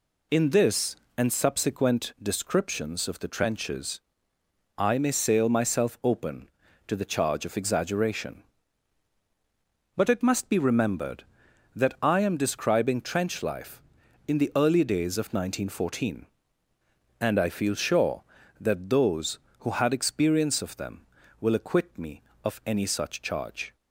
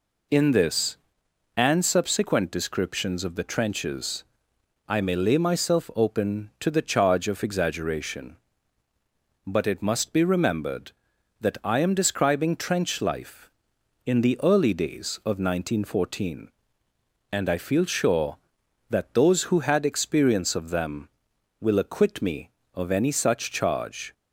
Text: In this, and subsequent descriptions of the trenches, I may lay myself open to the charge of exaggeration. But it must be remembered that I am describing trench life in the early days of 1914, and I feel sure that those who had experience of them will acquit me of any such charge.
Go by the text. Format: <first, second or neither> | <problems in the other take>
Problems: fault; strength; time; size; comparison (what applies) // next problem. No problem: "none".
second | says "sail" for "lay"; at 5.1 s